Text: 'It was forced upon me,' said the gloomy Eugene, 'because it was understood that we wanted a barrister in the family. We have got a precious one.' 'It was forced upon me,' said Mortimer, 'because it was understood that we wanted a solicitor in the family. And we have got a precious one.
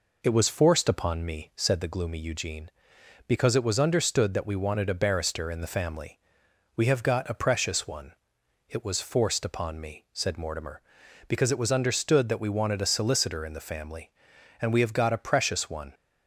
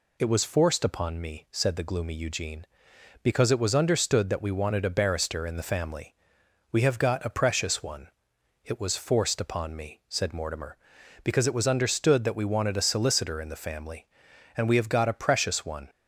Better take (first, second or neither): second